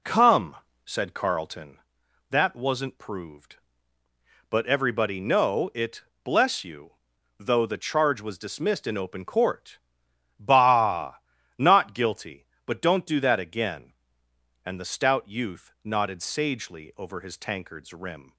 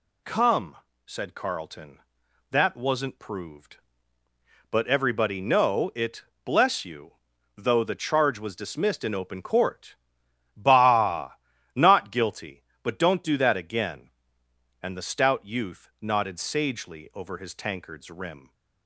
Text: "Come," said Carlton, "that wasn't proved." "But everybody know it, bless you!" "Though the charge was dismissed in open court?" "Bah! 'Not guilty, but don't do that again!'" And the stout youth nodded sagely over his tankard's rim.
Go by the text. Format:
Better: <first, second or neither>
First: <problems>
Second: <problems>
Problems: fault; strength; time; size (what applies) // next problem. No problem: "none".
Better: second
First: starts louder than the rest; slight; until 1.7 s; 3 dB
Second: none